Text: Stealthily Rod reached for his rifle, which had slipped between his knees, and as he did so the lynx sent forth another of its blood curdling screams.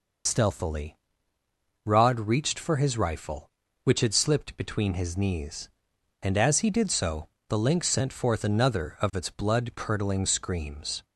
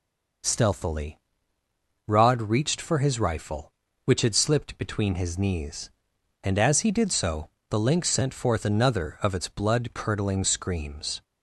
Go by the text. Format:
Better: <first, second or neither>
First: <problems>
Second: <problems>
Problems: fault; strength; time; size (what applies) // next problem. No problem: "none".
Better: second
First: loses the start of "Stealthily"; at 0.2 s; 55 ms // pauses between "Stealthily" and "Rod"; noticeable; at 0.9 s; 0.86 s long // pauses between "so" and "the"; slight; at 7.2 s; 0.20 s long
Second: pauses between "Stealthily" and "Rod"; noticeable; at 1.1 s; 0.86 s long // pauses between "so" and "the"; slight; at 7.4 s; 0.20 s long